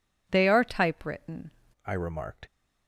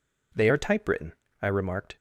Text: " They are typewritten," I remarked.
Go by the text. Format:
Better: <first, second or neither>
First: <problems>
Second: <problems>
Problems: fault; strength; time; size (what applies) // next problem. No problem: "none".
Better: second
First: changes voice from "They" to "typewritten"; from 0.3 to 1.5 s; 1.2 s long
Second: none